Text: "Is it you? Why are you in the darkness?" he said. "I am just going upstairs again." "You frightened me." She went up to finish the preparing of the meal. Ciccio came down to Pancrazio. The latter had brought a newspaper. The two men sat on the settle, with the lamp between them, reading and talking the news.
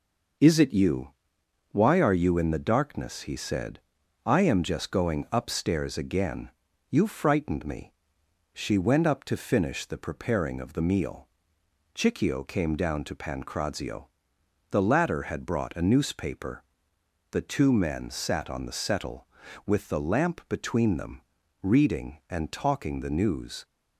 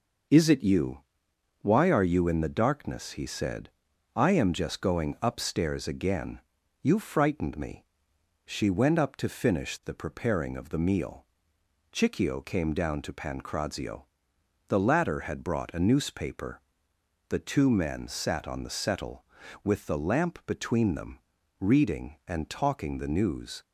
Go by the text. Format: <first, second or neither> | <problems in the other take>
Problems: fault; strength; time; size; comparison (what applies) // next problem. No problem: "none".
neither | none